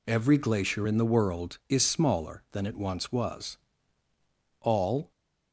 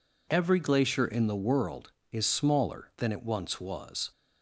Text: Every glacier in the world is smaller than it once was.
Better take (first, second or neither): second